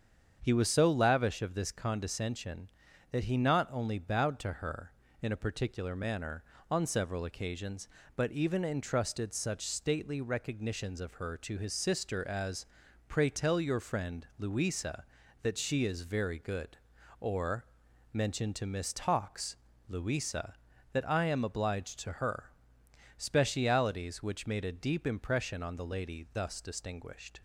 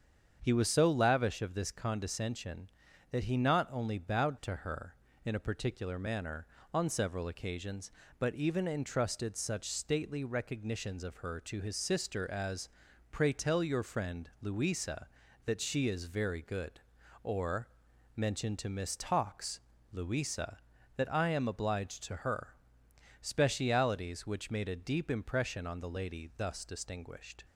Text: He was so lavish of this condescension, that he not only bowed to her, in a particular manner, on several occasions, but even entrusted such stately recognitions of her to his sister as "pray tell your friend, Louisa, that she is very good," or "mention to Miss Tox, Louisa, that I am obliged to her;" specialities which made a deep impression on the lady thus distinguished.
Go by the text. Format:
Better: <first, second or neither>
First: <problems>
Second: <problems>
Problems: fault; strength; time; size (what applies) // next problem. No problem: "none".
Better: neither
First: starts louder than the rest; strong; until 1.4 s; 7.5 dB // pauses between "as" and "pray"; noticeable; at 12.6 s; 0.46 s long // pauses between "or" and "mention"; noticeable; at 17.6 s; 0.48 s long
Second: starts louder than the rest; strong; until 1.4 s; 7.5 dB // pauses between "as" and "pray"; noticeable; at 12.6 s; 0.46 s long // pauses between "or" and "mention"; noticeable; at 17.6 s; 0.48 s long